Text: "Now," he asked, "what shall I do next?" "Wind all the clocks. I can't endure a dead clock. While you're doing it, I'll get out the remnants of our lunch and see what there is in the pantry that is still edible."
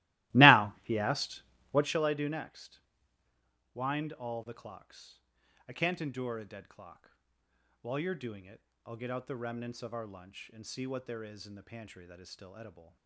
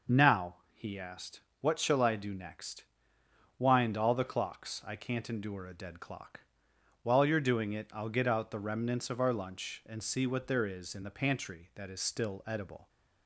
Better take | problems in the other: second | starts louder than the rest; strong; until 2.0 s; 18 dB

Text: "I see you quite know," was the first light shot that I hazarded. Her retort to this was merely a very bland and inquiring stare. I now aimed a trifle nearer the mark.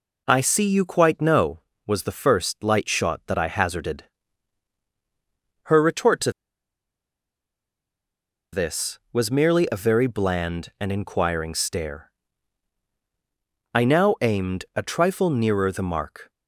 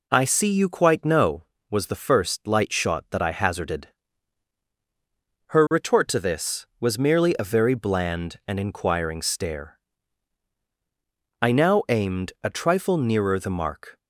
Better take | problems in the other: second | pauses between "to" and "this"; strong; at 6.3 s; 2.2 s long

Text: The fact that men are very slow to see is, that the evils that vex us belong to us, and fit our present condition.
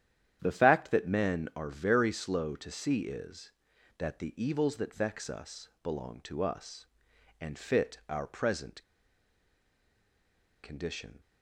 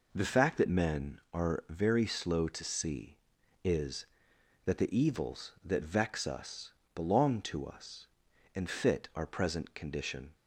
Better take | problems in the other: second | starts louder than the rest; strong; until 1.4 s; 10 dB // pauses between "us" and "belong"; slight; at 5.6 s; 0.16 s long; slight in the second // pauses between "present" and "condition"; strong; at 8.8 s; 1.8 s long

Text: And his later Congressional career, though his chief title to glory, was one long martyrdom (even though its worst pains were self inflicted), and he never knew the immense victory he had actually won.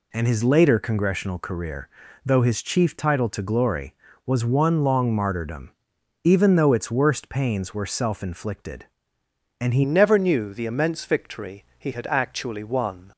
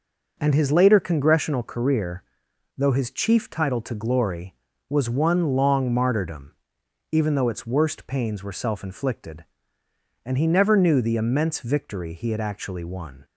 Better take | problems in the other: second | changes voice at "never"; from 9.8 s on; 3.3 s long // pauses between "victory" and "he"; slight; at 11.6 s; 0.16 s long

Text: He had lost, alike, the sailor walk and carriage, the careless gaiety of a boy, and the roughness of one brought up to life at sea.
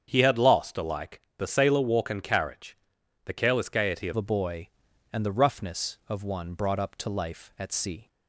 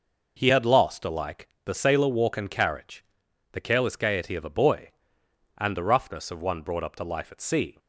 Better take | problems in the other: second | starts louder than the rest; strong; until 1.0 s; 7.5 dB // changes voice at "a"; from 4.1 s on; 3.9 s long

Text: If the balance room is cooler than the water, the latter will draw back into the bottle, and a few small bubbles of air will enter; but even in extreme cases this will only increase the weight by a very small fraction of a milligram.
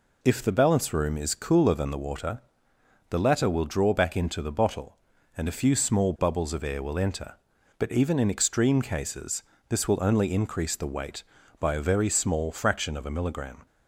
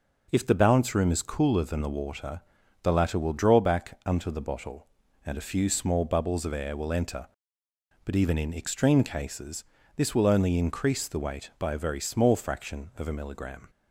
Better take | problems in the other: first | says "unto" for "into"; at 4.0 s // pauses between "cases" and "this"; slight; at 9.6 s; 0.32 s long; slight in the first

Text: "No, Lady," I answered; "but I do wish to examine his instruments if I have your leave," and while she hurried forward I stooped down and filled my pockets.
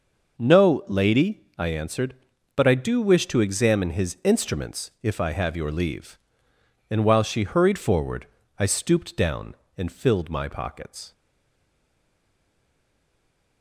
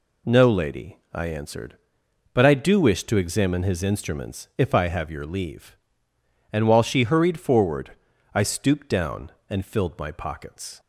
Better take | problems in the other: second | pauses between "forward" and "I"; slight; at 8.2 s; 0.34 s long; also in the second // stays silent after the last word; from 11.1 s on; 2.5 s long

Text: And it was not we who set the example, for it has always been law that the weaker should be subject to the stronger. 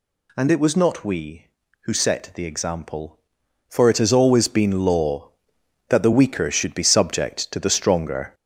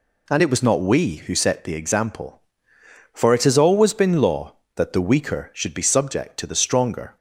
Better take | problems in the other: second | gets louder; slight; throughout; 3 dB

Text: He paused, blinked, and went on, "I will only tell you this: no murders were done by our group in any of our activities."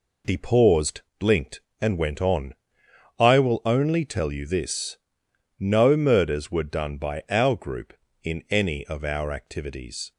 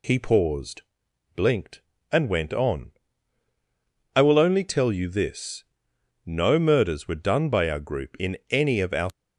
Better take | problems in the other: first | stops before "activities"; at 9.1 s

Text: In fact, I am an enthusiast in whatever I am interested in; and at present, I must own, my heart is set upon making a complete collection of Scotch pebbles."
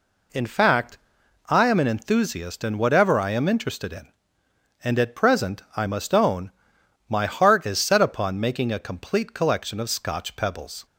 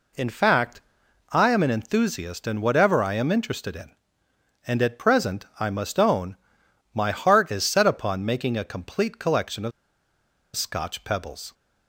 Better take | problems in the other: first | pauses between "of" and "Scotch"; noticeable; at 9.7 s; 0.84 s long

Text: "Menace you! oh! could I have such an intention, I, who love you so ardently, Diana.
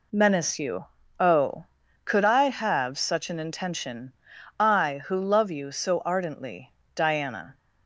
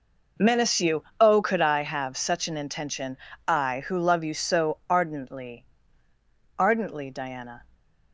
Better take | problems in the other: first | says "ardently" twice; at 6.5 s

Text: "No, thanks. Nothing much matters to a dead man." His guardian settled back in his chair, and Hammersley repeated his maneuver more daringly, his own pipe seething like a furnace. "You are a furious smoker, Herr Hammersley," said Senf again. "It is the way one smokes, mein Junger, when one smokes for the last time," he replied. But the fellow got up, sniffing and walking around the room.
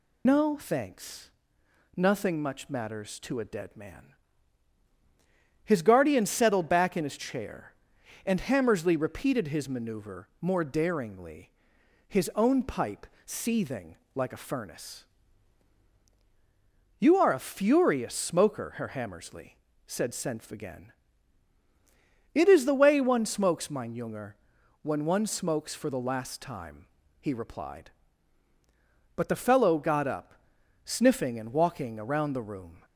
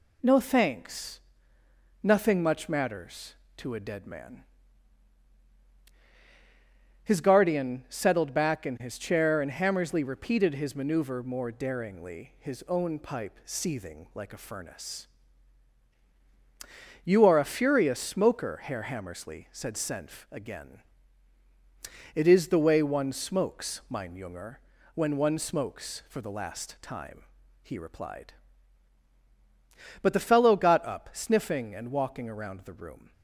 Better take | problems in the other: second | loses the start of "No"; at 0.2 s; 55 ms // pauses between "pipe" and "seething"; slight; at 13.0 s; 0.18 s long // pauses between "seething" and "like"; slight; at 13.9 s; 0.18 s long

